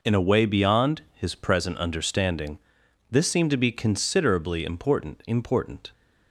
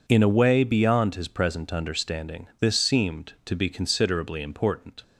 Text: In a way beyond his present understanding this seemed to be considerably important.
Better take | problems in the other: second | pauses between "understanding" and "this"; noticeable; at 2.5 s; 0.54 s long // says "important" twice; at 5.2 s

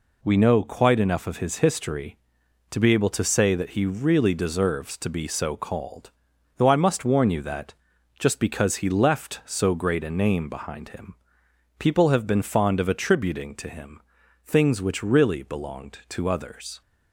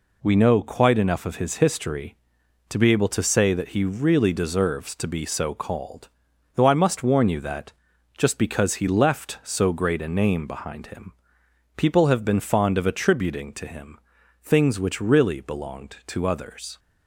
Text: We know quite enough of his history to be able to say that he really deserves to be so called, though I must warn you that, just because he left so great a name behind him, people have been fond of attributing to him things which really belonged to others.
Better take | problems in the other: neither | pauses between "him" and "things"; noticeable; the same in both

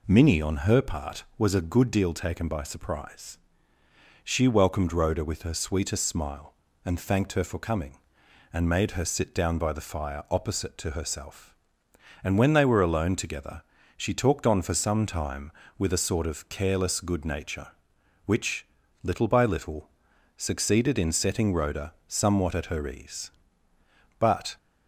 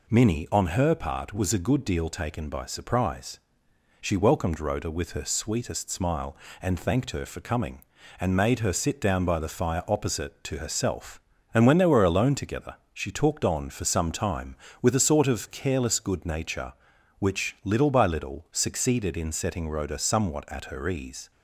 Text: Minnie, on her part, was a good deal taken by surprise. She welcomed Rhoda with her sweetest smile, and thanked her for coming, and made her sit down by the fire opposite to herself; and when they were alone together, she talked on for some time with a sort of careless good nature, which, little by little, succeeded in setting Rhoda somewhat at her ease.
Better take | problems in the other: second | goes on to say "But"; slight; from 24.1 s on; 0.38 s long

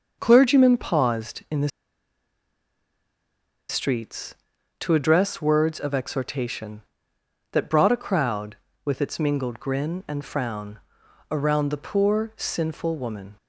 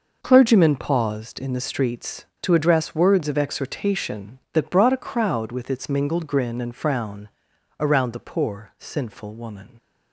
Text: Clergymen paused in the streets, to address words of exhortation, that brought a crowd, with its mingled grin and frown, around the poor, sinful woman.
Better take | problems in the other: second | starts louder than the rest; until 1.2 s; 6.5 dB // pauses between "the" and "streets"; strong; at 1.6 s; 1.9 s long

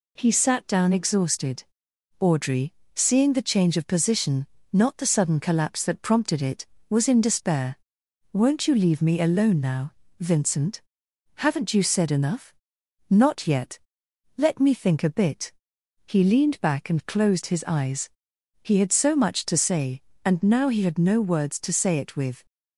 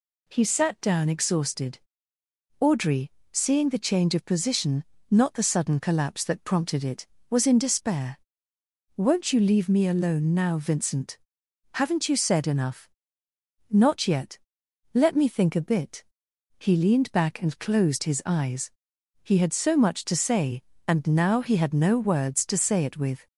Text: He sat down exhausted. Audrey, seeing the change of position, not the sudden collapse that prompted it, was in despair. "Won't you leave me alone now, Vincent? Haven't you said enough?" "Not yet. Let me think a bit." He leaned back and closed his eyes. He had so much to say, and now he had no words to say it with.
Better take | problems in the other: neither | none

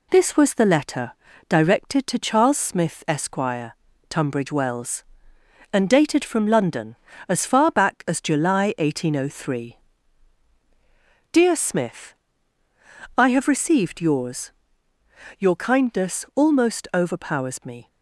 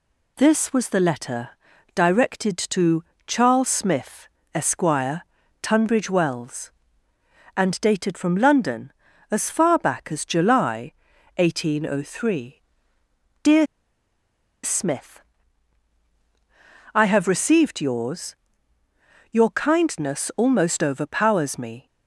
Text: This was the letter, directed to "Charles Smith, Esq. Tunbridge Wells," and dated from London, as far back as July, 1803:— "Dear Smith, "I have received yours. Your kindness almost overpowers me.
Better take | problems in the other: first | pauses between "to" and "Charles"; slight; at 3.0 s; 0.22 s long // pauses between "Dear" and "Smith"; at 13.6 s; 0.99 s long

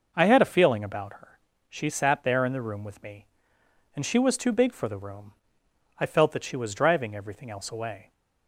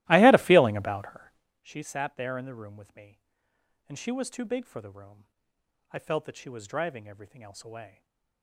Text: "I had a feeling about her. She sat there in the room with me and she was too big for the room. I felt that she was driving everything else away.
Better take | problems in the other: first | starts louder than the rest; strong; until 1.6 s; 17 dB // stays silent after the last word; slight; from 7.8 s on; 0.6 s long

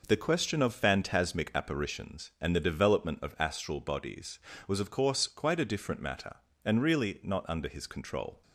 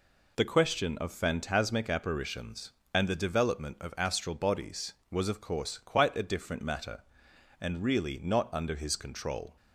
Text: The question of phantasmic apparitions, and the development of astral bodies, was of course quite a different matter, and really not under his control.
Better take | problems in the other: neither | none

